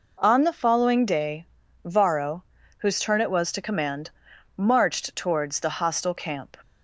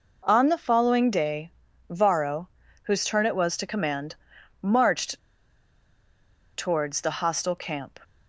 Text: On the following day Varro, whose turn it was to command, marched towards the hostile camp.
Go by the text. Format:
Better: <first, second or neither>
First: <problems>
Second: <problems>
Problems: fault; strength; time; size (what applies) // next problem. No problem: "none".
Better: first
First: pauses between "day" and "Varro"; at 1.4 s; 0.38 s long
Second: pauses between "day" and "Varro"; at 1.5 s; 0.38 s long // pauses between "marched" and "towards"; strong; at 5.1 s; 1.3 s long